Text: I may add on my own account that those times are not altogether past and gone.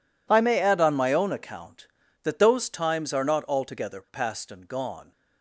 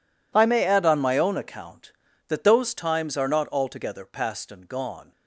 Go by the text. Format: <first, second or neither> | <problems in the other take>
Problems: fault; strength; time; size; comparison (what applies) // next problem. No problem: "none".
neither | none